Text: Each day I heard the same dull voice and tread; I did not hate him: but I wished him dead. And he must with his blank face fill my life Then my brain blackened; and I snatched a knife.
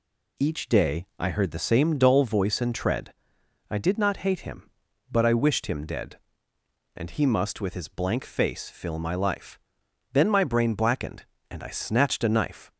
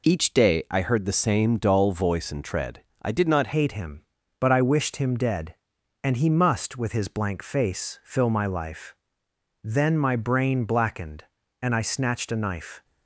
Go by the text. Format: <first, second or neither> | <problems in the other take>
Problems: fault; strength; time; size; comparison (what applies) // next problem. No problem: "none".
first | changes voice at "hate"; from 3.5 s on; 9.3 s long // pauses between "life" and "Then"; noticeable; at 8.9 s; 0.70 s long; noticeable in the first